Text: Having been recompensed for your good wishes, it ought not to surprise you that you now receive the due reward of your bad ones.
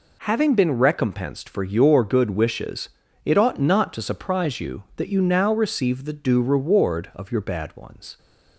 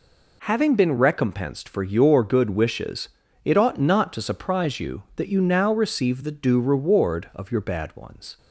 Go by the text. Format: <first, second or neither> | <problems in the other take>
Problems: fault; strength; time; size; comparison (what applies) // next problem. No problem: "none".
neither | none